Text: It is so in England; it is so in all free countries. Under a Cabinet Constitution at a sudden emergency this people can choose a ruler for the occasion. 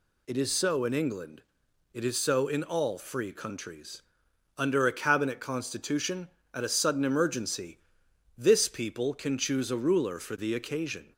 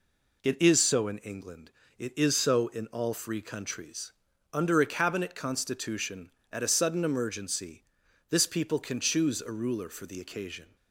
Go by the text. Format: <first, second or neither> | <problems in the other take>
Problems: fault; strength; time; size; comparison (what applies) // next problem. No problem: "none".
neither | pauses between "emergency" and "this"; noticeable; the same in both